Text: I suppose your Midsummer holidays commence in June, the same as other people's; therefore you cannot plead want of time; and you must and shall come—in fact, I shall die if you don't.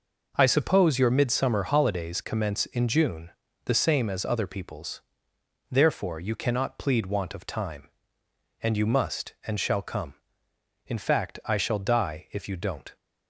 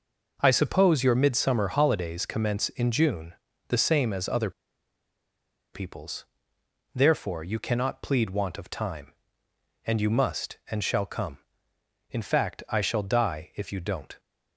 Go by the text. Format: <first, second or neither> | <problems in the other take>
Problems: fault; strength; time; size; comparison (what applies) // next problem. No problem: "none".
first | pauses between "other" and "people's"; at 4.5 s; 1.2 s long